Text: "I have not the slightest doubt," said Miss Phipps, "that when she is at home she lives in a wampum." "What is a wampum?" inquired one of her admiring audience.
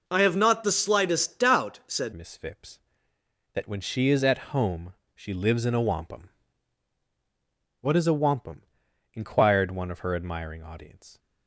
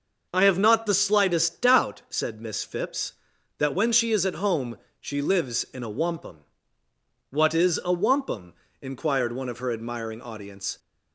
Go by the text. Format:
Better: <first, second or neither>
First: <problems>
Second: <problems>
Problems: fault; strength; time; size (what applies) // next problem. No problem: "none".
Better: second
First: changes voice at "Miss"; from 2.1 s on; 9.0 s long // pauses between "home" and "she"; slight; at 4.9 s; 0.22 s long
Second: pauses between "home" and "she"; slight; at 4.7 s; 0.22 s long